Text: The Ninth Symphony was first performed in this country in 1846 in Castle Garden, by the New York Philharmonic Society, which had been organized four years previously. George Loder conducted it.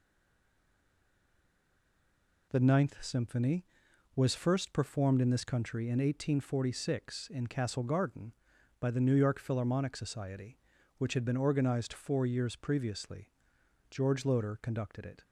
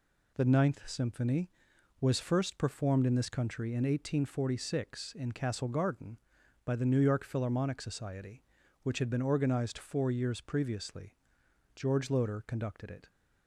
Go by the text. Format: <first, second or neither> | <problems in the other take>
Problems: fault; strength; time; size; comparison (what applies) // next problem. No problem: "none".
second | stays silent before the first word; until 2.5 s; 2.5 s long